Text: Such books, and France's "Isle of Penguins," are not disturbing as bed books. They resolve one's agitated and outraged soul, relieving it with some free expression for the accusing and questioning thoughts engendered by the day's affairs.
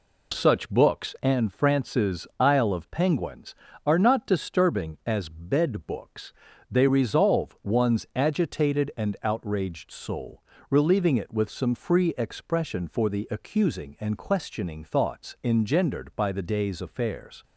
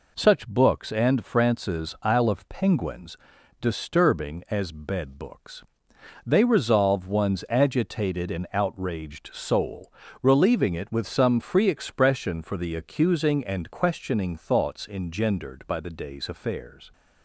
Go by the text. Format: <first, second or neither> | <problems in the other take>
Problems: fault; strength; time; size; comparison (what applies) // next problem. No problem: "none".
first | skips "are not"; at 3.3 s